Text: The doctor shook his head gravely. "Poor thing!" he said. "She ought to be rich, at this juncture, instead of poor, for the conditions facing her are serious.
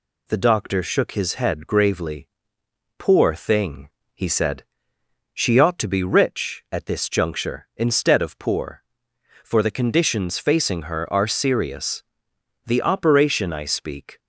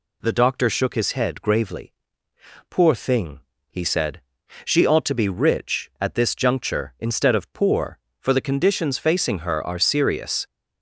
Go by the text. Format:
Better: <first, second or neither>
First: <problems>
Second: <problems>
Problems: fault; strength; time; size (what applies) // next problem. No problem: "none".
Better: second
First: goes on to say "The operation I speak"; from 12.6 s on; 1.5 s long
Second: none